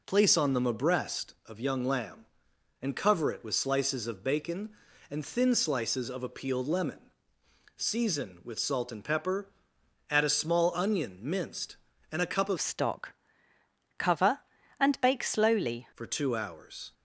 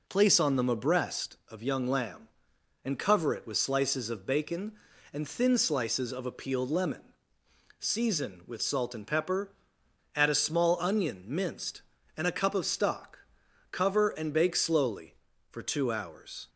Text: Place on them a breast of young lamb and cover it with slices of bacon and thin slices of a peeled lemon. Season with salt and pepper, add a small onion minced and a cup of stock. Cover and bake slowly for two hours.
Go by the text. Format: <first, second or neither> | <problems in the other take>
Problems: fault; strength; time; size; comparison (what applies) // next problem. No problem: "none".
second | changes voice from "stock" to "slowly"; from 12.6 to 15.8 s; 3.2 s long